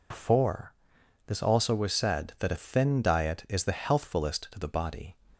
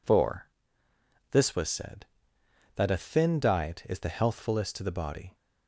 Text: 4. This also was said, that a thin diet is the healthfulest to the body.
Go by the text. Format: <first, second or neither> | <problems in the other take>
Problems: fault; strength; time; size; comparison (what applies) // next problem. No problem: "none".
first | skips "also"; at 1.5 s